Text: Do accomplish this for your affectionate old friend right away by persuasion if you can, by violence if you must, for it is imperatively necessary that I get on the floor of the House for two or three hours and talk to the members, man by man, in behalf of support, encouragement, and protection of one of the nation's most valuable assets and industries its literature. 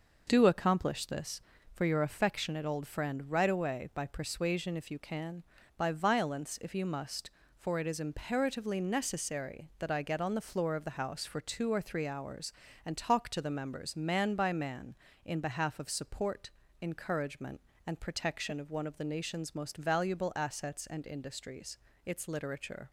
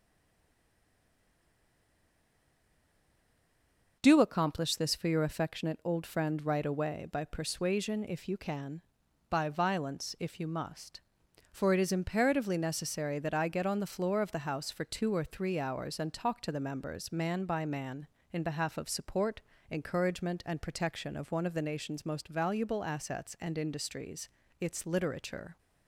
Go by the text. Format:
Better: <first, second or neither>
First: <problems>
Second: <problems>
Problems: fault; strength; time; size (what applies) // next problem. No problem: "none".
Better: first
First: pauses between "industries" and "its"; slight; at 21.7 s; 0.26 s long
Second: stays silent before the first word; strong; until 3.9 s; 3.9 s long // pauses between "industries" and "its"; slight; at 24.2 s; 0.32 s long